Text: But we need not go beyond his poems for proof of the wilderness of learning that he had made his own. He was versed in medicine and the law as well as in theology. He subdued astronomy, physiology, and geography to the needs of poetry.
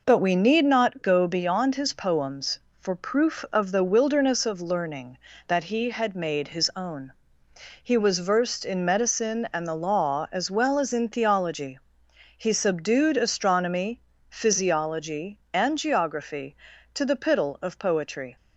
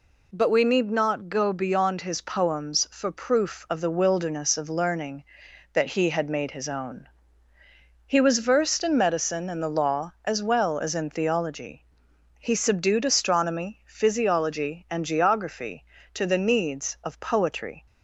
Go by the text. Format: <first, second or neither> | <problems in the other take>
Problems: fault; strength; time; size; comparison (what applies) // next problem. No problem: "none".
second | says "piddle" for "needs"; at 17.1 s